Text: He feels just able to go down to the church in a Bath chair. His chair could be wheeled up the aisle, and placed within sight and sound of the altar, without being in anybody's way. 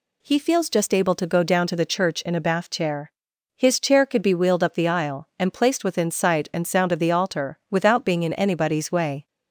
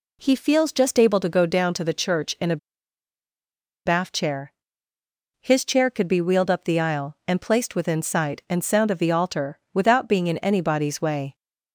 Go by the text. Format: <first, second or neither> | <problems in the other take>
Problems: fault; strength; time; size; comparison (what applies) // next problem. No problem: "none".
first | pauses between "a" and "Bath"; strong; at 2.5 s; 1.2 s long